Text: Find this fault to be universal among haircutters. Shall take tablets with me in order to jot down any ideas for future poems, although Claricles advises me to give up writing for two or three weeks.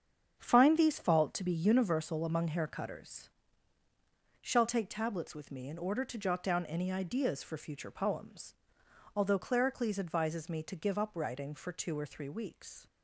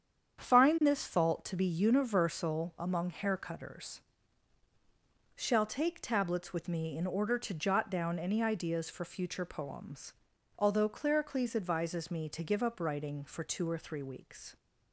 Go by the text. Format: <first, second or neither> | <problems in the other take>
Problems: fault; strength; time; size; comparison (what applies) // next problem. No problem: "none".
second | starts louder than the rest; strong; until 1.3 s; 7.5 dB; strong in the second // says "these" for "this"; at 0.7 s